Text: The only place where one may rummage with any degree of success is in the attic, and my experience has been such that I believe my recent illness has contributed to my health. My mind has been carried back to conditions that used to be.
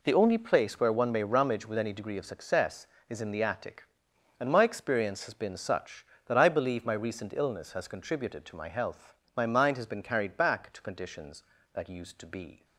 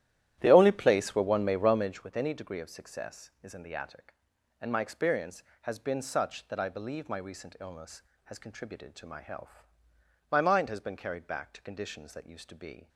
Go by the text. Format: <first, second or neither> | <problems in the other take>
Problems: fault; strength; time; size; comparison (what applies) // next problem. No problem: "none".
first | starts louder than the rest; strong; until 2.1 s; 12.5 dB